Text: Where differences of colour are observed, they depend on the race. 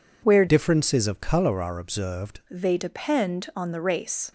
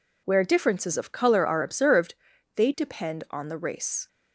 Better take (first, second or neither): second